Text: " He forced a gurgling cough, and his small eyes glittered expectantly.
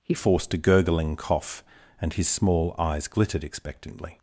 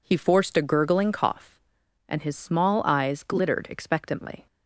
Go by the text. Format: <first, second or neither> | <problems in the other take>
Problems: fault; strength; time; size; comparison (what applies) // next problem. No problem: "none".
second | changes voice at "forced"; from 0.1 s on; 4.0 s long